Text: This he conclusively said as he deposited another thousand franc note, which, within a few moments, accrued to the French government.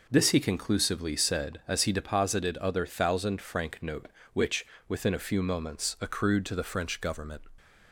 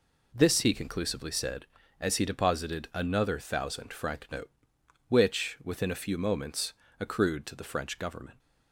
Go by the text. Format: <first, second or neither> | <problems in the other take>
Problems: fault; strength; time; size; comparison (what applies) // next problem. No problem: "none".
second | says "other" for "another"; at 2.5 s